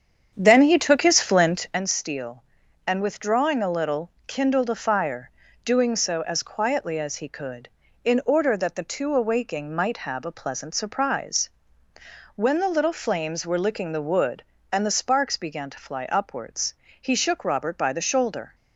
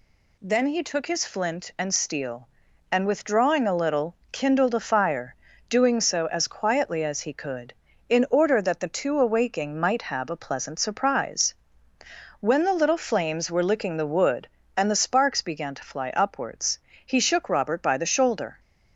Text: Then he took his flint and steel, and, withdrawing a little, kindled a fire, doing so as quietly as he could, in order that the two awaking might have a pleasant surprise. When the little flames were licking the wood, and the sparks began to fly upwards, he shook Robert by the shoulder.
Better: second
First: starts louder than the rest; strong; until 1.9 s; 8 dB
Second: none

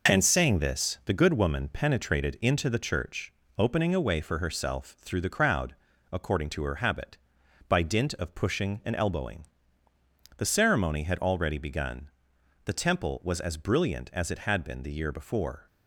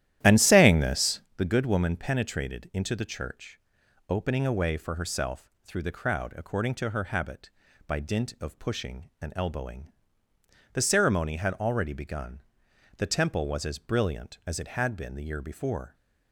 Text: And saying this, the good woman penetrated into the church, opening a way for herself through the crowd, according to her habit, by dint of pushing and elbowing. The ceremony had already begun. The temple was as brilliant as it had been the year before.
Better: first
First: none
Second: starts louder than the rest; strong; until 1.3 s; 12.5 dB

